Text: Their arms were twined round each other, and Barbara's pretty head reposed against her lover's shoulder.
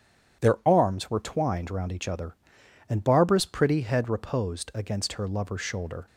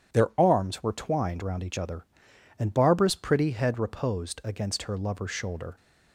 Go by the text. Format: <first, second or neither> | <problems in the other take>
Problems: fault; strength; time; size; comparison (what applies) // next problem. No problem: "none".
neither | starts louder than the rest; strong; the same in both